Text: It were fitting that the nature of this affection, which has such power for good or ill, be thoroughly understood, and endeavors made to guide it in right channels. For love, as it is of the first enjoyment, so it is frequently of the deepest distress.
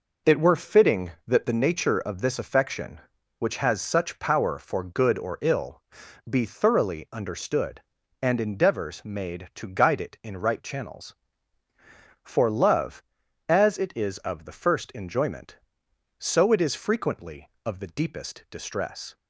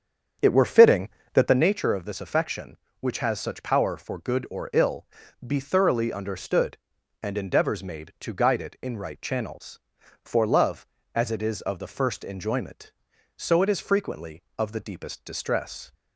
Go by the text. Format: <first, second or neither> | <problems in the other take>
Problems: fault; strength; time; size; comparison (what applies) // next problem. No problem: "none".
first | starts louder than the rest; strong; until 1.7 s; 7.5 dB